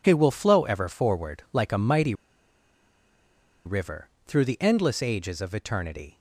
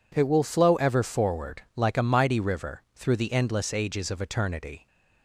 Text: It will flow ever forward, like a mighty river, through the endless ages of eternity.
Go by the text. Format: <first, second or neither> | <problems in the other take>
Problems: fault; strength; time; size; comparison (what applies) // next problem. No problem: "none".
second | pauses between "mighty" and "river"; strong; at 2.1 s; 1.5 s long